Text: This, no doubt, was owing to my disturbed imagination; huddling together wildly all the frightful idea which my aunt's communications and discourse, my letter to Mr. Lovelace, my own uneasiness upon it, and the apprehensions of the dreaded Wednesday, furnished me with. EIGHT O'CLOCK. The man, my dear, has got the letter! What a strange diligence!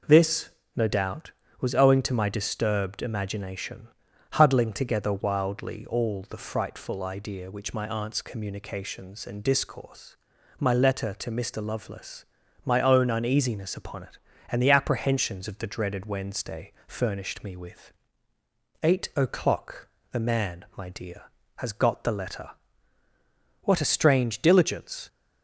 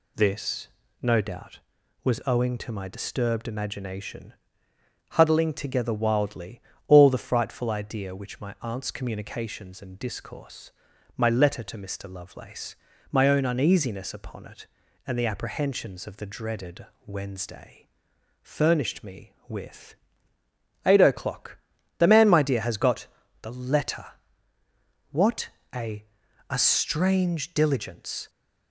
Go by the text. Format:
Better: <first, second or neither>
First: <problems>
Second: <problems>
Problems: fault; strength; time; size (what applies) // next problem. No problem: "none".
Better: first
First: none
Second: pauses between "wildly" and "all"; slight; at 6.6 s; 0.26 s long // pauses between "dreaded" and "Wednesday"; slight; at 16.8 s; 0.20 s long // pauses between "got" and "the"; slight; at 23.0 s; 0.34 s long // pauses between "What" and "a"; slight; at 25.4 s; 0.26 s long // says "a" twice; at 26.4 s